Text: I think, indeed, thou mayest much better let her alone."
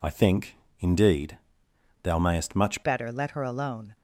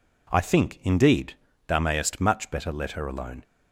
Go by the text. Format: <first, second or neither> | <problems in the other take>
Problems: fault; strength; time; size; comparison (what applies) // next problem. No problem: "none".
second | changes voice at "better"; from 2.8 s on; 1.1 s long